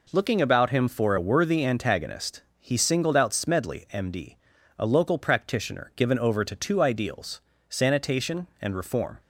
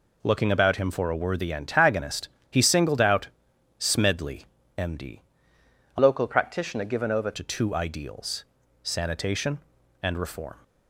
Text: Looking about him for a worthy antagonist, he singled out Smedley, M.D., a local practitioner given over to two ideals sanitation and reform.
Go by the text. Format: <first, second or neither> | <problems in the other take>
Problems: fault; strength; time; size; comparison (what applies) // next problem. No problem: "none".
first | pauses between "out" and "Smedley"; noticeable; at 3.2 s; 0.50 s long // changes voice from "local" to "over"; from 5.9 to 7.3 s; 1.4 s long // pauses between "ideals" and "sanitation"; at 8.4 s; 0.38 s long; slight in the first